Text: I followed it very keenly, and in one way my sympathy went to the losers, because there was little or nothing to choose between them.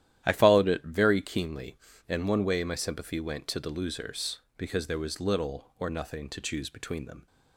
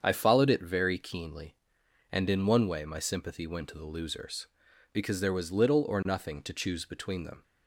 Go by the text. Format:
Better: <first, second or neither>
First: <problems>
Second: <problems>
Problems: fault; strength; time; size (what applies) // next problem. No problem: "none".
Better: second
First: starts louder than the rest; strong; until 1.2 s; 12 dB // skips "in"; at 2.2 s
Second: starts louder than the rest; strong; until 1.0 s; 7.5 dB